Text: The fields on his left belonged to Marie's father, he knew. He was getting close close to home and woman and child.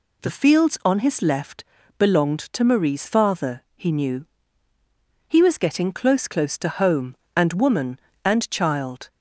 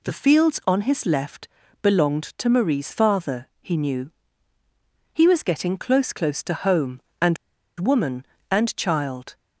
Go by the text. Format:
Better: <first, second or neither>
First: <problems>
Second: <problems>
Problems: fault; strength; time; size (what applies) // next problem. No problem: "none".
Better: first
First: pauses between "left" and "belonged"; slight; at 1.6 s; 0.34 s long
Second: pauses between "left" and "belonged"; slight; at 1.4 s; 0.34 s long // pauses between "and" and "woman"; at 7.3 s; 0.43 s long